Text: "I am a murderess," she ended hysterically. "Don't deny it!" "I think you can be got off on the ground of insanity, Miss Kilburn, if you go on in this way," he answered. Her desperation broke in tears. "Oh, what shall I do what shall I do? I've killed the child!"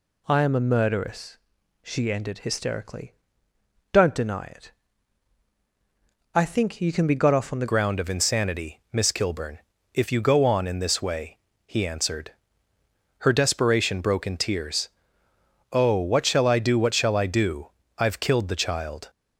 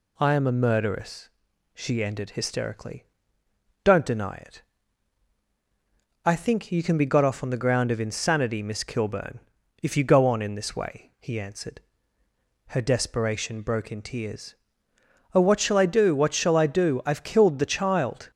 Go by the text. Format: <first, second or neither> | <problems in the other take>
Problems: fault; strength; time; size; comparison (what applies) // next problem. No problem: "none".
second | changes voice at "ground"; from 7.6 s on; 11.4 s long